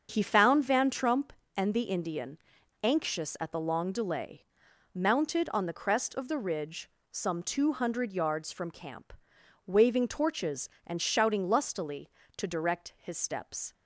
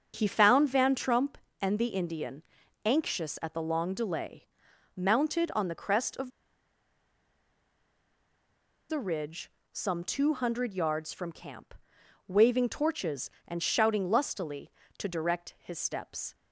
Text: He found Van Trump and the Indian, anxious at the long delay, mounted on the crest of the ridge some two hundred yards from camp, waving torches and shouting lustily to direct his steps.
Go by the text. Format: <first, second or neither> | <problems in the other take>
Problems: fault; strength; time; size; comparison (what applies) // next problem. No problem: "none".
first | starts louder than the rest; until 1.1 s; 7 dB; also in the first // pauses between "of" and "the"; strong; at 6.3 s; 2.5 s long // pauses between "ridge" and "some"; slight; at 9.4 s; 0.24 s long; slight in the first